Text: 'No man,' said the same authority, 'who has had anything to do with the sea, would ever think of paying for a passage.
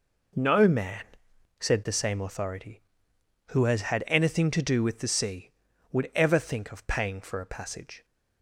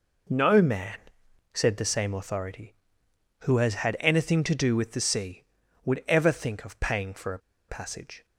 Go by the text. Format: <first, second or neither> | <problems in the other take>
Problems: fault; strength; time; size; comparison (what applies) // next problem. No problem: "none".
first | pauses between "a" and "passage"; slight; at 7.3 s; 0.30 s long